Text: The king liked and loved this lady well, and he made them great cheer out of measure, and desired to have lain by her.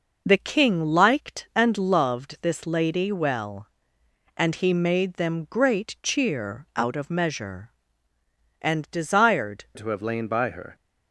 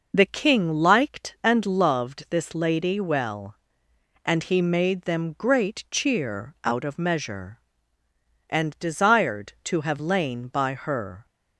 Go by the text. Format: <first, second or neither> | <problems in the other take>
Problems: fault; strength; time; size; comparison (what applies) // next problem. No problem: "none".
second | changes voice at "to"; from 9.7 s on; 1.0 s long